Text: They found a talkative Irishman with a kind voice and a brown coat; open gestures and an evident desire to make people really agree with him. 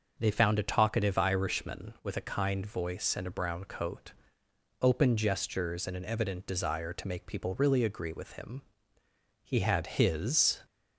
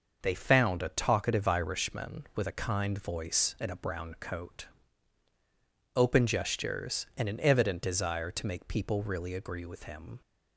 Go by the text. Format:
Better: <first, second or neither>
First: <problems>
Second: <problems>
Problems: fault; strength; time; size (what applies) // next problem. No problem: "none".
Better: second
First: goes on to say "He had his"; noticeable; from 9.4 s on; 1.1 s long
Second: none